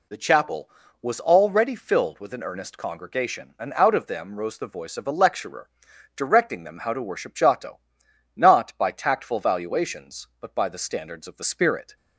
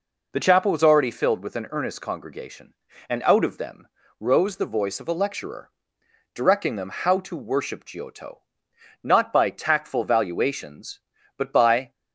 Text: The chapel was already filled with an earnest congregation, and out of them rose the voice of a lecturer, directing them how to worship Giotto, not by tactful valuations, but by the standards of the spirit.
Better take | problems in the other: first | pauses between "them" and "rose"; slight; at 3.8 s; 0.32 s long // stops before "the standards of the spirit"; at 11.9 s

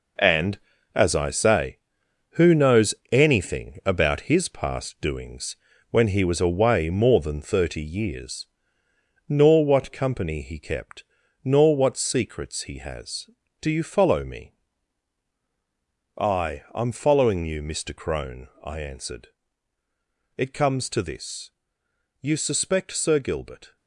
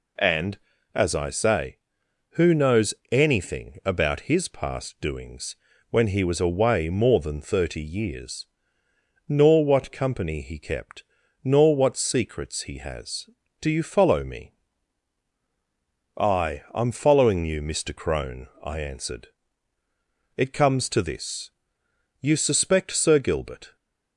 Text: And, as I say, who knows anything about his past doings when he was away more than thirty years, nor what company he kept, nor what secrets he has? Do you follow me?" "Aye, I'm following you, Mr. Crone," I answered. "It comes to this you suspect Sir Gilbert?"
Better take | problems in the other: second | gets quieter; strong; throughout; 8.5 dB // pauses between "knows" and "anything"; slight; at 2.9 s; 0.18 s long; slight in the second // pauses between "doings" and "when"; slight; at 5.5 s; 0.34 s long; slight in the second // pauses between "this" and "you"; noticeable; at 21.5 s; 0.70 s long; noticeable in the second

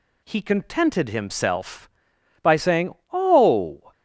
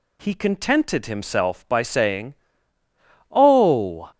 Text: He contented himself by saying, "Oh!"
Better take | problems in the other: neither | none

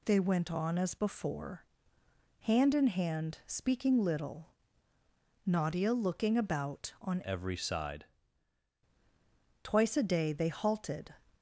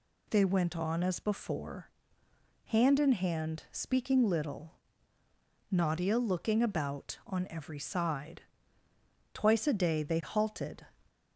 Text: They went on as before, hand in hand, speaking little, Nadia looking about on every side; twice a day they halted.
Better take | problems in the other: second | changes voice from "every" to "side"; from 7.2 to 8.0 s; 0.8 s long

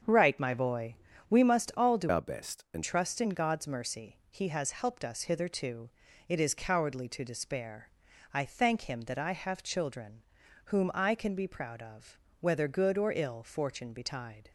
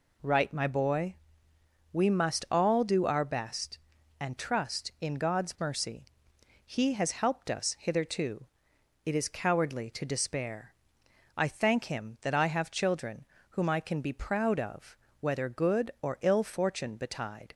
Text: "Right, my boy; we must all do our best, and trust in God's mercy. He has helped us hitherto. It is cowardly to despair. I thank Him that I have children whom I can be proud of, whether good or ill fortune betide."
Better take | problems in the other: second | starts louder than the rest; until 1.3 s; 7 dB // changes voice from "our" to "and"; from 2.0 to 2.8 s; 0.8 s long // pauses between "children" and "whom"; noticeable; at 10.2 s; 0.46 s long; slight in the second

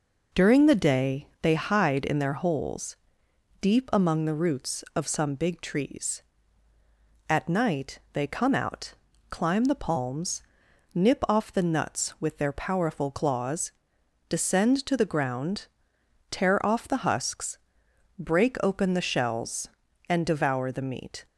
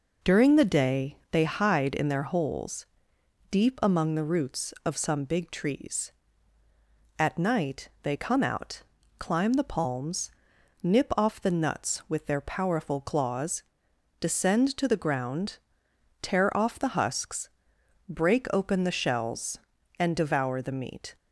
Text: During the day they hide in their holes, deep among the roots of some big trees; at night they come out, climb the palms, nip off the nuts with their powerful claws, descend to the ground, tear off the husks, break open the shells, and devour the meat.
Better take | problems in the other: neither | none

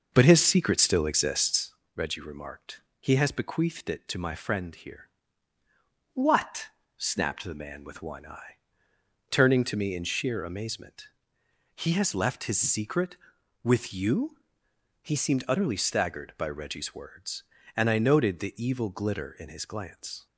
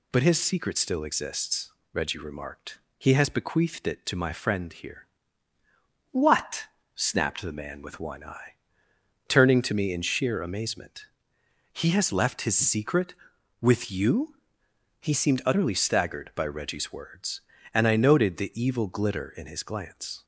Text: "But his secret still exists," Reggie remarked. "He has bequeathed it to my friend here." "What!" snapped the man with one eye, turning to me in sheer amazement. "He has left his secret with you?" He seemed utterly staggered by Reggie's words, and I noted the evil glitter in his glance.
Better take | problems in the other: second | starts louder than the rest; noticeable; until 1.7 s; 6 dB

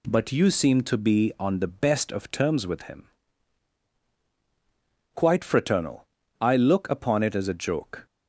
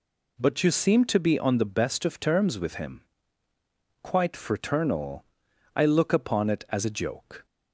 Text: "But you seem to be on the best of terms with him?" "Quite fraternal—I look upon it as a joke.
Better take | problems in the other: neither | none

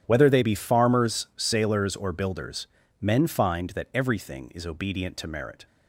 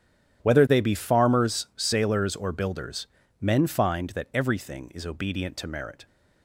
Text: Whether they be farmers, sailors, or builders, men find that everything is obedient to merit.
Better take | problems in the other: neither | starts louder than the rest; strong; the same in both

